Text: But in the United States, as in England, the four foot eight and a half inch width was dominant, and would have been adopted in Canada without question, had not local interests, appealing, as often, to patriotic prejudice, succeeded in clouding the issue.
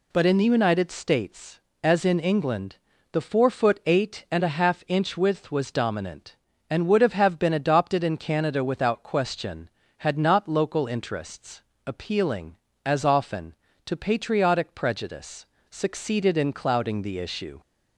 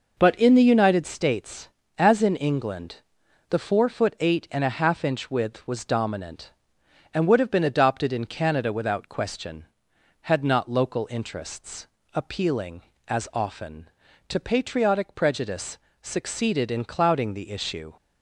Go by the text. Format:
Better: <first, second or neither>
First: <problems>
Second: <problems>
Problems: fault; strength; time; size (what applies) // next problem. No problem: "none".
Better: second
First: says "have" twice; at 7.1 s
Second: none